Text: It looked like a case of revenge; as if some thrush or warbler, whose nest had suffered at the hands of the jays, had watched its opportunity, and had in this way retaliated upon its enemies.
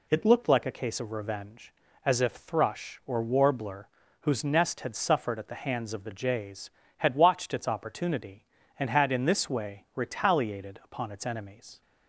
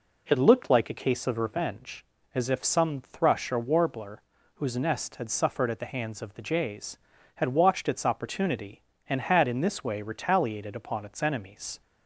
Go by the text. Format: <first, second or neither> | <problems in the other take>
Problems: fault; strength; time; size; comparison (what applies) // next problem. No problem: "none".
second | skips "some"; at 2.3 s